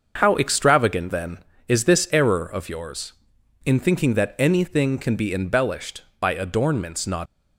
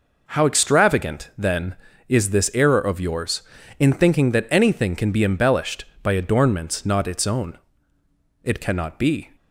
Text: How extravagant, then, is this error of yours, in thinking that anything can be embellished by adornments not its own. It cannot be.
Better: second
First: starts louder than the rest; until 1.1 s; 6.5 dB // stops before "its own It cannot be"; at 7.2 s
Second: none

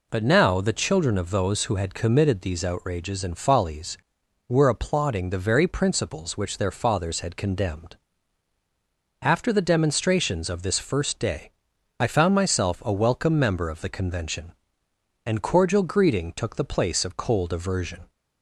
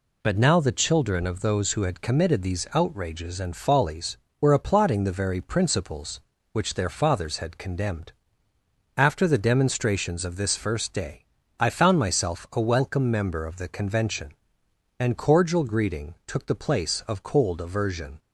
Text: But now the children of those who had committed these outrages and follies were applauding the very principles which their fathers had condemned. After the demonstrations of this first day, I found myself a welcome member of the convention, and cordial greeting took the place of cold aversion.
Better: neither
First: none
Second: none

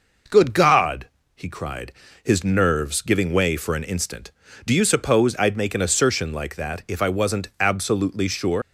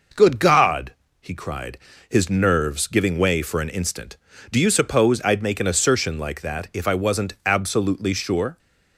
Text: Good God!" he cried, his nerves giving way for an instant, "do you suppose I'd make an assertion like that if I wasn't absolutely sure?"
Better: second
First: leaves "sure" unfinished; at 8.6 s; 105 ms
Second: none

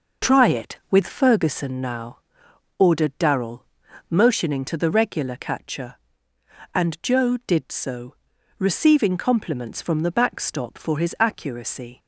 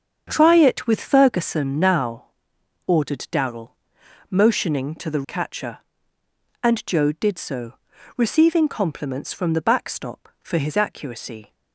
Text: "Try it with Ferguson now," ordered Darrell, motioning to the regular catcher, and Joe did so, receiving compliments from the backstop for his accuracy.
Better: first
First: none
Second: starts louder than the rest; strong; until 1.2 s; 7 dB // skips "regular"; at 5.2 s

